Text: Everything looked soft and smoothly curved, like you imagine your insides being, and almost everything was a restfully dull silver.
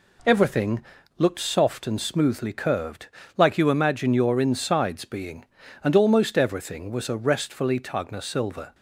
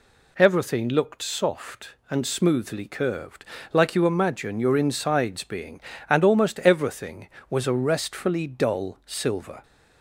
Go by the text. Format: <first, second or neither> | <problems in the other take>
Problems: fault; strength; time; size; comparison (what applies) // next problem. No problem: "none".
second | pauses between "Everything" and "looked"; slight; at 0.8 s; 0.32 s long // says "tagna" for "dull"; at 7.7 s